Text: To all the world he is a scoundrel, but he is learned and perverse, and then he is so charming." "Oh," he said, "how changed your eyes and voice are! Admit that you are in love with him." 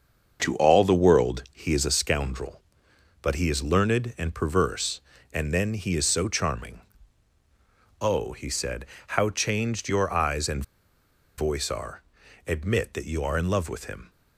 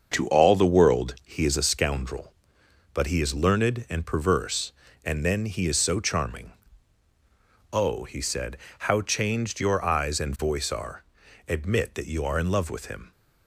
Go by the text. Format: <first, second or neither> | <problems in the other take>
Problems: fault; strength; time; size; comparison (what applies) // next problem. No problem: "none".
second | starts louder than the rest; until 1.4 s; 6.5 dB; also in the second // pauses between "and" and "voice"; noticeable; at 10.6 s; 0.75 s long